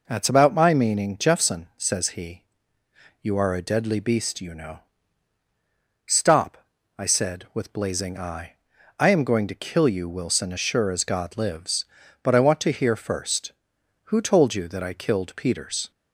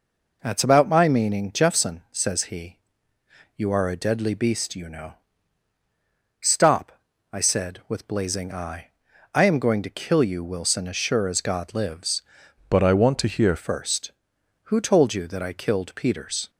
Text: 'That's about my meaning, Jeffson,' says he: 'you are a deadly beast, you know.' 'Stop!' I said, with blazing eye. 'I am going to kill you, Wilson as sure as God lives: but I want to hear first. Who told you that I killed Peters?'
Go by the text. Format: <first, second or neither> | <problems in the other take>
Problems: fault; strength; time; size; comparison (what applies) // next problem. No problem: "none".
first | changes voice from "but" to "hear"; from 12.7 to 13.5 s; 0.8 s long